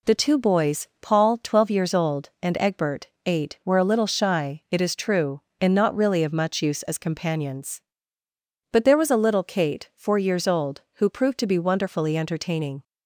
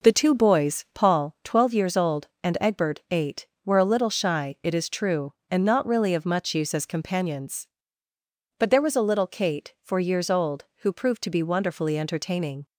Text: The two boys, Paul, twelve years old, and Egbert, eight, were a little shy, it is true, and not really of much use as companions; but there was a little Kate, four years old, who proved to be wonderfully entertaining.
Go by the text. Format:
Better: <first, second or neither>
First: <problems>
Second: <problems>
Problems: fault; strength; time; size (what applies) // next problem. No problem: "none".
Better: first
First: none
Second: starts louder than the rest; noticeable; until 1.3 s; 5.5 dB